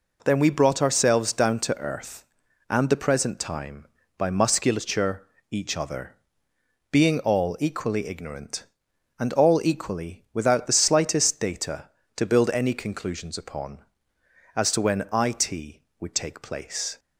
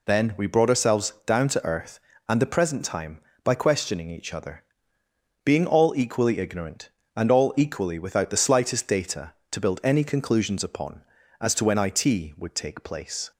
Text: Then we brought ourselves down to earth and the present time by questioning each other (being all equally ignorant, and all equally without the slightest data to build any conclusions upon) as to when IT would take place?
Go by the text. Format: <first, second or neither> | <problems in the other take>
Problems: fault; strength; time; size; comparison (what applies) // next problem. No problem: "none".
second | says "musculature" for "questioning"; at 4.2 s